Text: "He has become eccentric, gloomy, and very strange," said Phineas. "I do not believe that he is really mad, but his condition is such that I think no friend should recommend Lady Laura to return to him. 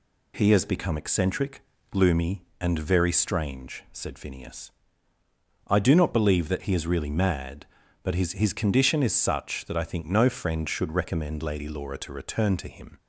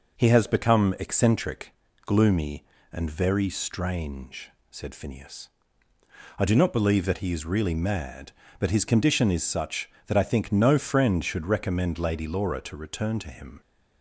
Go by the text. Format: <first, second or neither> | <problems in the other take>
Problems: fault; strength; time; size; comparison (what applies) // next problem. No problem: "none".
second | says "his" twice; at 8.3 s